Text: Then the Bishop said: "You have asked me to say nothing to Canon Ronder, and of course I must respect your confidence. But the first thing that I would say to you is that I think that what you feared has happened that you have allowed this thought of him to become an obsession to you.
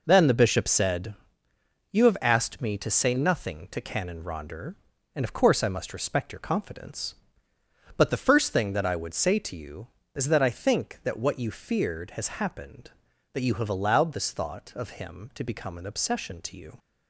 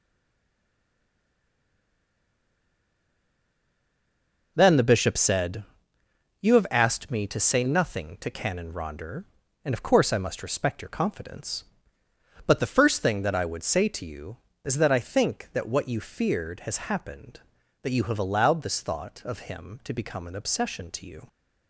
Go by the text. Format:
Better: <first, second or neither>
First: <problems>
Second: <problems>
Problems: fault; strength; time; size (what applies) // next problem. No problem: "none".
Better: first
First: none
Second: stays silent before the first word; strong; until 4.5 s; 4.5 s long